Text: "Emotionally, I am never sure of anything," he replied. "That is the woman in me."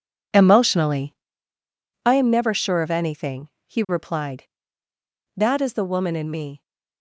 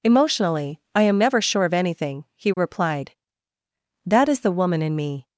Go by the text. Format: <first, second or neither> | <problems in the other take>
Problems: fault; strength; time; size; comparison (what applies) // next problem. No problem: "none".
second | gets quieter; strong; throughout; 12.5 dB